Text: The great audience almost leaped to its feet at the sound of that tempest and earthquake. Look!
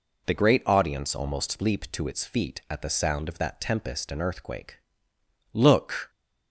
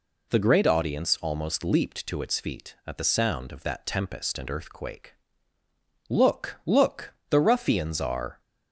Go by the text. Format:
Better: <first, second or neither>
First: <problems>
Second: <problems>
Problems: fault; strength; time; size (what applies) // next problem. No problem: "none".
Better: first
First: none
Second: goes on to say "Look the ruffians are"; strong; from 6.6 s on; 1.7 s long